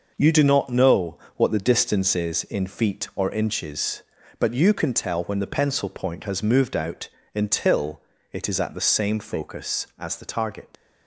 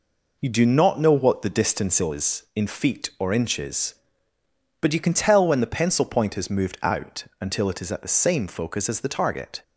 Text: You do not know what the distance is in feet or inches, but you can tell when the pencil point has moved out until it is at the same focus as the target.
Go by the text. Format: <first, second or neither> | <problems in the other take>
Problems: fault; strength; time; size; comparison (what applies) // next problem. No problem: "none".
second | pauses between "know" and "what"; slight; at 1.1 s; 0.20 s long // pauses between "out" and "until"; slight; at 7.0 s; 0.26 s long; slight in the second // pauses between "until" and "it"; slight; at 7.9 s; 0.32 s long // leaves "target" unfinished; at 10.7 s; 85 ms